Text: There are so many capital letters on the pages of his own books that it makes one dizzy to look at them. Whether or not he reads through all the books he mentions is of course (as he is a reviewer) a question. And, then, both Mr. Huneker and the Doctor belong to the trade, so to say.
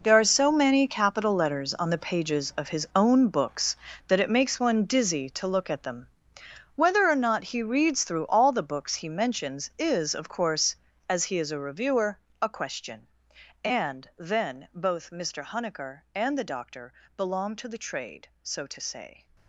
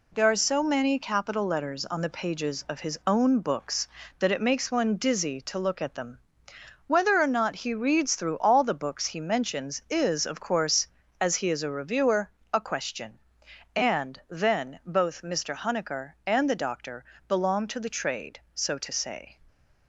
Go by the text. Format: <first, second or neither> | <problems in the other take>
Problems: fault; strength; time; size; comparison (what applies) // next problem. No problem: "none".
second | gets quieter; strong; throughout; 14 dB // pauses between "Doctor" and "belong"; slight; at 16.9 s; 0.22 s long; slight in the second